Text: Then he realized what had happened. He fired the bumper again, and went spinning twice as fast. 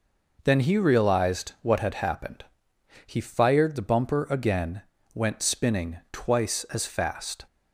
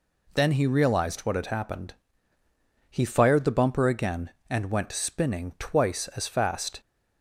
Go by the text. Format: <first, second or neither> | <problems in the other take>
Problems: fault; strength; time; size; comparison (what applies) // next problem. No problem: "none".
second | skips "and"; at 4.9 s